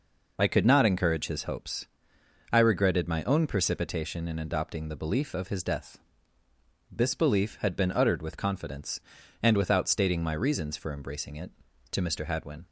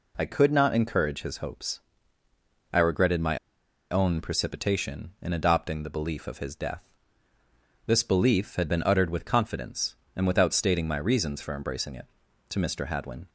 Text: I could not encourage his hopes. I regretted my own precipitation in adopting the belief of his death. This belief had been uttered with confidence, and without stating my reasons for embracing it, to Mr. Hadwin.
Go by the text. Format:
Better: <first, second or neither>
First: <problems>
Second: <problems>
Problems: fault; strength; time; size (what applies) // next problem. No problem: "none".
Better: first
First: none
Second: pauses between "my" and "own"; noticeable; at 3.3 s; 0.53 s long